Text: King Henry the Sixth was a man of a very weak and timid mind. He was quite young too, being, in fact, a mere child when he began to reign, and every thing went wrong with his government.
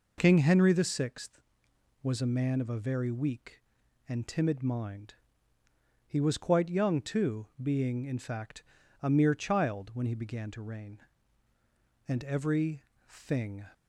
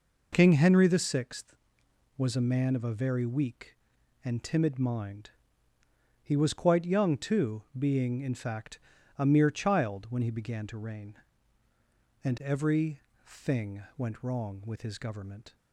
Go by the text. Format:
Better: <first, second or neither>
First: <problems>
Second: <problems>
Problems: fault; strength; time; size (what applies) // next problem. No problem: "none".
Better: second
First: pauses between "every" and "thing"; slight; at 12.8 s; 0.26 s long // stops before "went wrong with his government"; at 13.7 s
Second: pauses between "every" and "thing"; slight; at 12.9 s; 0.26 s long